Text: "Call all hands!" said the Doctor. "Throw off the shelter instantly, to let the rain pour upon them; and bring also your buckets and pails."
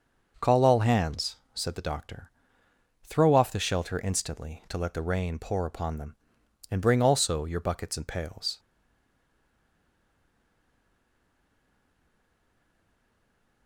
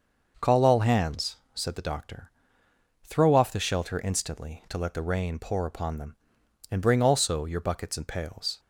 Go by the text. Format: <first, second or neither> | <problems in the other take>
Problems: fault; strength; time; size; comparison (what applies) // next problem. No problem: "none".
second | starts louder than the rest; noticeable; until 1.5 s; 6 dB; noticeable in the second // stays silent after the last word; strong; from 8.5 s on; 5.1 s long